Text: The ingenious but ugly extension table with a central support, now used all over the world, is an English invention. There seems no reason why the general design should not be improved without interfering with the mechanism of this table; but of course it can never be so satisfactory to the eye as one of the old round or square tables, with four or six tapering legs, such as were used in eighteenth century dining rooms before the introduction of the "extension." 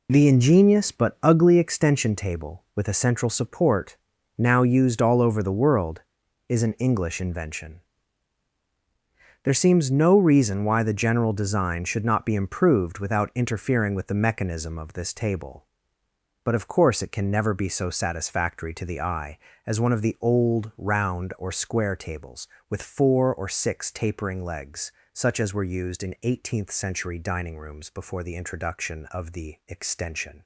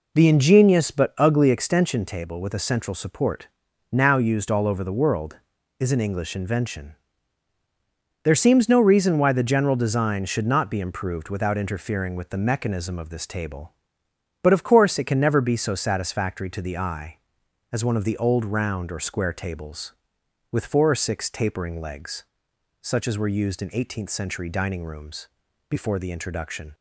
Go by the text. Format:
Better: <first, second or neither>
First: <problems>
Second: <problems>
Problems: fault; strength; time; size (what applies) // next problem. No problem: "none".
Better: first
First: none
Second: pauses between "rooms" and "before"; at 25.2 s; 0.42 s long // stops before "of the extension"; at 26.7 s